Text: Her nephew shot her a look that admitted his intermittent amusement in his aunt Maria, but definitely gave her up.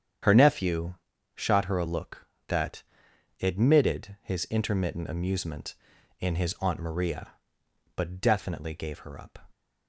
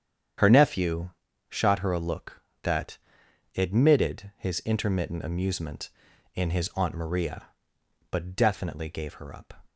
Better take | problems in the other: neither | starts louder than the rest; strong; the same in both // pauses between "nephew" and "shot"; the same in both // pauses between "that" and "admitted"; noticeable; the same in both

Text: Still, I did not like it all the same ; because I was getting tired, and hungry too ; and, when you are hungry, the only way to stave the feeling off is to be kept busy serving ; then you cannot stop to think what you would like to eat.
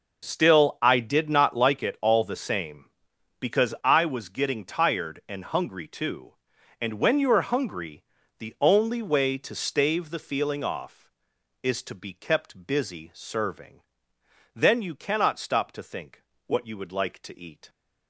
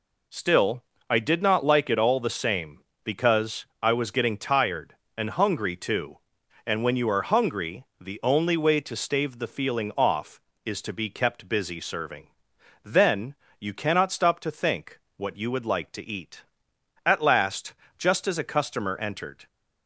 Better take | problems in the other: first | pauses between "because" and "I"; slight; at 3.6 s; 0.18 s long // pauses between "then" and "you"; slight; at 13.3 s; 0.24 s long // pauses between "think" and "what"; slight; at 14.9 s; 0.18 s long; slight in the first // goes on to say "At last just as a customer entered"; strong; from 17.0 s on; 2.4 s long

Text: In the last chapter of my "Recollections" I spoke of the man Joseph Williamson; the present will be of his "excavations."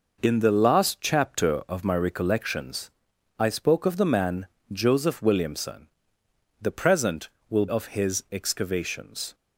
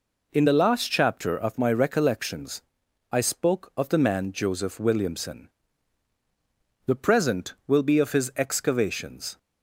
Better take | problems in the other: second | pauses between "Recollections" and "I"; noticeable; at 2.8 s; 0.48 s long; noticeable in the second // pauses between "man" and "Joseph"; slight; at 4.4 s; 0.24 s long // skips "be"; at 7.6 s

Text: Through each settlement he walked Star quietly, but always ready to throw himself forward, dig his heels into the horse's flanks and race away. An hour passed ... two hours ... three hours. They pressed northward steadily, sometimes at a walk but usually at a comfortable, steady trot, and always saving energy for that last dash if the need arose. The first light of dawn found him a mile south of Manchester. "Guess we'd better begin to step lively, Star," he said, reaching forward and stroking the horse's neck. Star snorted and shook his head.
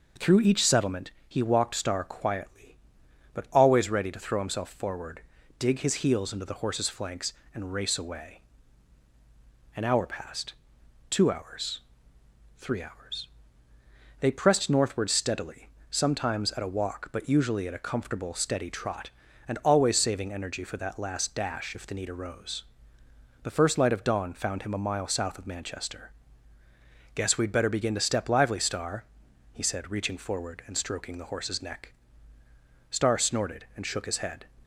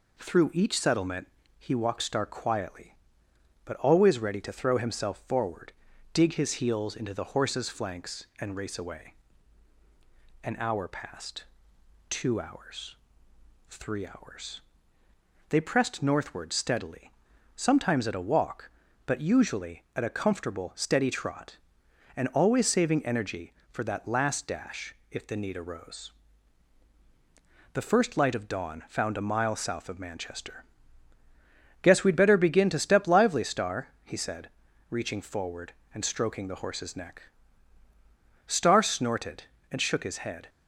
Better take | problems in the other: first | pauses between "settlement" and "he"; slight; at 1.2 s; 0.30 s long; slight in the first // pauses between "dash" and "if"; slight; at 24.9 s; 0.16 s long // skips "him"; at 29.1 s

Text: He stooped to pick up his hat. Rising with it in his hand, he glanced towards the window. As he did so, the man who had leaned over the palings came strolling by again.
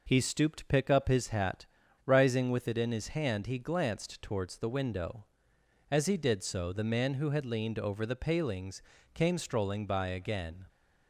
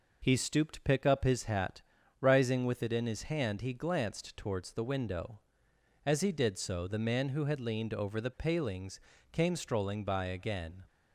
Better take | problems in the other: neither | pauses between "palings" and "came"; slight; the same in both

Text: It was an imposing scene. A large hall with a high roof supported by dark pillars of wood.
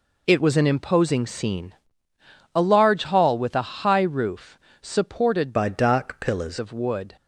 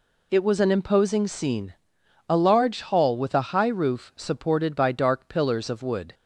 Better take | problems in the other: second | pauses between "roof" and "supported"; slight; at 4.5 s; 0.22 s long // changes voice from "by" to "pillars"; from 5.5 to 6.5 s; 1.0 s long

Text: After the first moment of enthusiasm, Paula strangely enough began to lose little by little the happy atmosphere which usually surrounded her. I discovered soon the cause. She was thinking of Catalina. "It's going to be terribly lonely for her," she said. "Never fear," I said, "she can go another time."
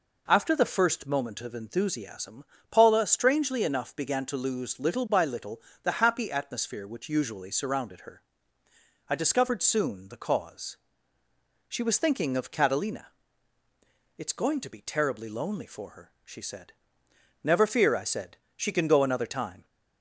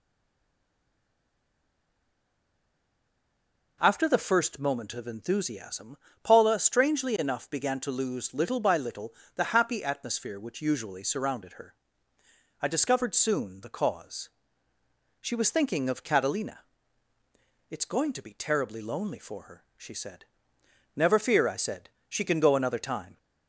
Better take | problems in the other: first | stays silent before the first word; strong; until 3.8 s; 3.8 s long // pauses between "little" and "the"; slight; at 9.1 s; 0.24 s long; slight in the first

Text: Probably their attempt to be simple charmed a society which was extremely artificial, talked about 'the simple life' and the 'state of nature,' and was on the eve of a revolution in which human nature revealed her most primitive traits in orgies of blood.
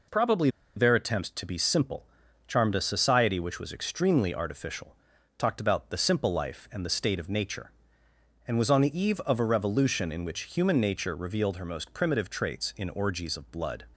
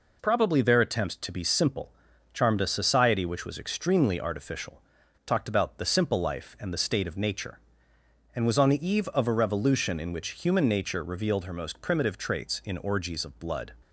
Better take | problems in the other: second | pauses between "Probably" and "their"; slight; at 0.4 s; 0.26 s long // pauses between "simple" and "charmed"; at 2.0 s; 0.40 s long; also in the second

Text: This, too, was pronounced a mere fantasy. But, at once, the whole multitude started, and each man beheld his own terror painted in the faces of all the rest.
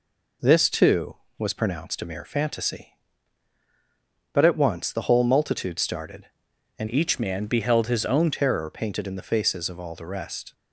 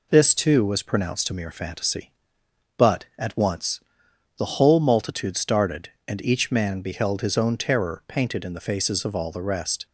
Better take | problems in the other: second | changes voice from "each" to "own"; from 6.8 to 8.3 s; 1.5 s long

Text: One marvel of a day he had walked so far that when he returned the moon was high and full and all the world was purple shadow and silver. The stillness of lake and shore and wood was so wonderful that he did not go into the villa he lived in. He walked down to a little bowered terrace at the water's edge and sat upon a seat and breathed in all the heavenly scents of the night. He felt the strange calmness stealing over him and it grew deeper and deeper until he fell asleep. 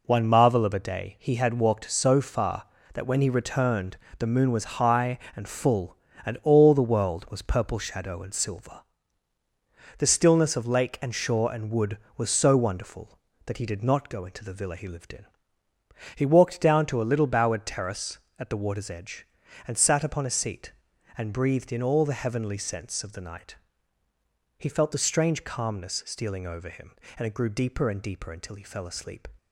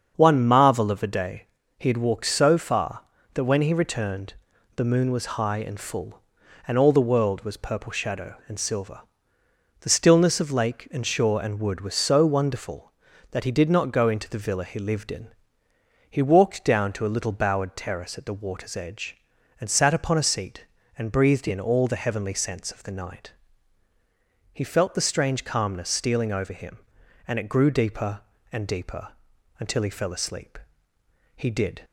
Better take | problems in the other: first | starts louder than the rest; until 1.1 s; 7 dB // pauses between "day" and "he"; slight; at 1.4 s; 0.34 s long // pauses between "returned" and "the"; at 4.3 s; 0.42 s long; slight in the first // pauses between "deeper" and "until"; noticeable; at 29.0 s; 0.50 s long // goes on to say "He did"; slight; from 31.3 s on; 0.46 s long

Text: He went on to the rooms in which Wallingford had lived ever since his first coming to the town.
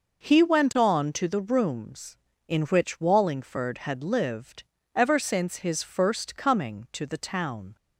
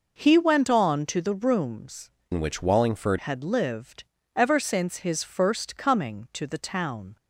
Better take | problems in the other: first | changes voice from "in" to "Wallingford"; from 2.3 to 3.1 s; 0.8 s long // pauses between "lived" and "ever"; slight; at 4.0 s; 0.32 s long; slight in the first

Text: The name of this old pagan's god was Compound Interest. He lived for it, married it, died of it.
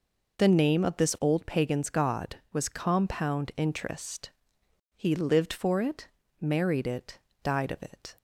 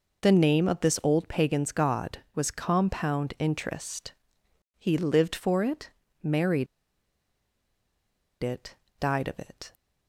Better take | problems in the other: first | pauses between "married" and "it"; strong; at 6.6 s; 1.7 s long

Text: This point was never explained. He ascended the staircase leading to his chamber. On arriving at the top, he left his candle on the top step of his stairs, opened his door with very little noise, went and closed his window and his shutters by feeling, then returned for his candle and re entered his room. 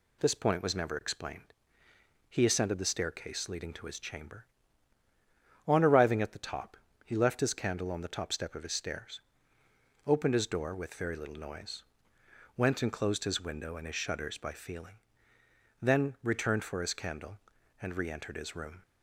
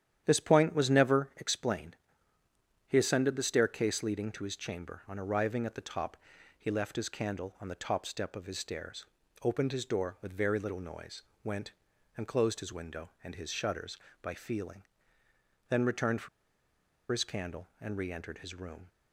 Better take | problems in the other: first | starts louder than the rest; strong; until 1.2 s; 10 dB // pauses between "for" and "his"; noticeable; at 16.2 s; 0.83 s long

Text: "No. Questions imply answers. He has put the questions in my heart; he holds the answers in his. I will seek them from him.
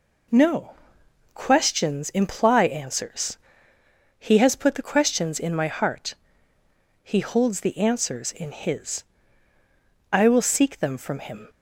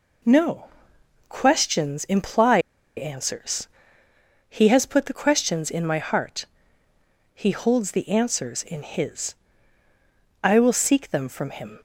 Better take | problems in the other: first | pauses between "imply" and "answers"; at 2.5 s; 0.38 s long

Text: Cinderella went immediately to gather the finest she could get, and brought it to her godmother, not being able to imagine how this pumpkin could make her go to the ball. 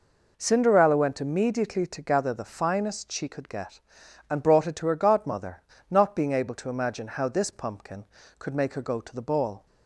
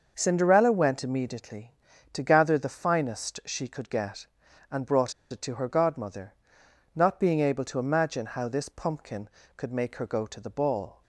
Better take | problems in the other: first | starts louder than the rest; noticeable; until 1.1 s; 6 dB // pauses between "brought" and "it"; slight; at 5.1 s; 0.18 s long

